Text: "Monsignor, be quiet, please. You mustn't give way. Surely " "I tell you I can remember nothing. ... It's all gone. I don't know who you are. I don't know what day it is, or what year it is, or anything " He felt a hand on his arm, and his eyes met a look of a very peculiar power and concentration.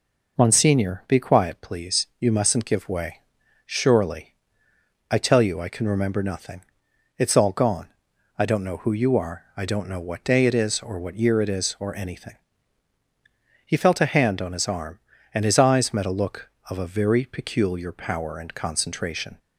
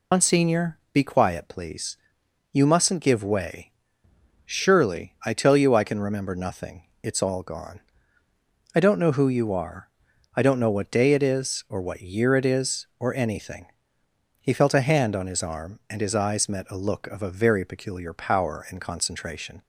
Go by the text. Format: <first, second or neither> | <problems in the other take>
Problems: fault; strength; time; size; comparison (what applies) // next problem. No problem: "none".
first | loses the start of "Monsignor"; at 0.1 s; 90 ms